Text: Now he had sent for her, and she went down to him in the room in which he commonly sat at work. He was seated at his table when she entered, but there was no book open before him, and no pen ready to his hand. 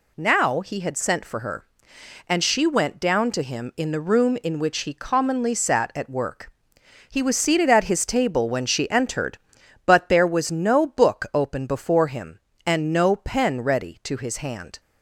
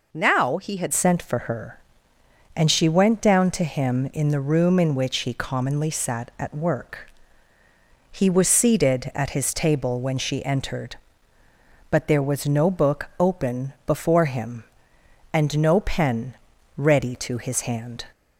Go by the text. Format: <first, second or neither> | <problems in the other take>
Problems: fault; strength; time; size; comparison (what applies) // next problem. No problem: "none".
first | changes voice at "sent"; from 0.9 s on; 17.1 s long // pauses between "pen" and "ready"; at 16.3 s; 0.40 s long